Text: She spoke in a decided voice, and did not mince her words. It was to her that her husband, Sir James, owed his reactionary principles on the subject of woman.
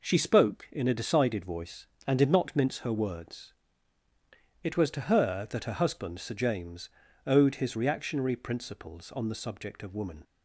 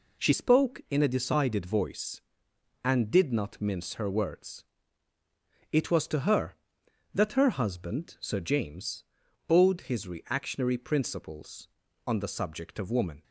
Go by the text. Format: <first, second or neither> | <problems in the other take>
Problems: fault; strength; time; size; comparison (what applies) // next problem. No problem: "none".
first | changes voice at "spoke"; from 0.3 s on; 12.9 s long